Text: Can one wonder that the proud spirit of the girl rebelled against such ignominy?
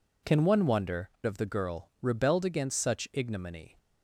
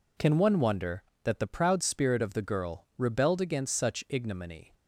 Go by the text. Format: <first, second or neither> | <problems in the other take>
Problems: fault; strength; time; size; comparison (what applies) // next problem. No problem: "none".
second | skips "that the proud spirit"; at 1.1 s